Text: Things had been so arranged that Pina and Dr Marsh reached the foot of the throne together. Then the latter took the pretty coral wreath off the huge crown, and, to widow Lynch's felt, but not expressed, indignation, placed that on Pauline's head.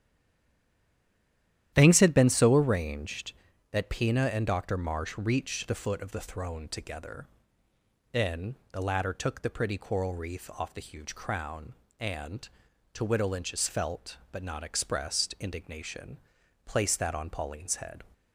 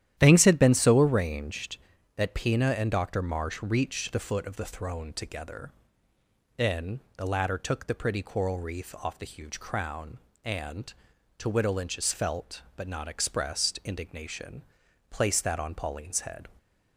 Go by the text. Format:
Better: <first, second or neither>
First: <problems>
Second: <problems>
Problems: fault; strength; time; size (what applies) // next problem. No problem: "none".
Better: second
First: stays silent before the first word; noticeable; until 1.7 s; 1.7 s long // starts louder than the rest; strong; until 2.7 s; 11.5 dB // pauses between "Then" and "the"; slight; at 8.5 s; 0.18 s long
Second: starts louder than the rest; strong; until 1.1 s; 11.5 dB // pauses between "Then" and "the"; slight; at 6.9 s; 0.18 s long